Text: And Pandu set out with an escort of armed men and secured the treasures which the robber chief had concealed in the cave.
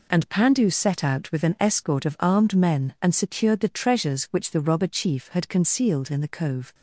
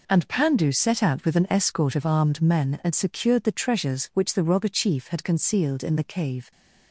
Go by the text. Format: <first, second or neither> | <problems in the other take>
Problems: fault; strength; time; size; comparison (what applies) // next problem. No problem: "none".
second | says "cove" for "cave"; at 6.2 s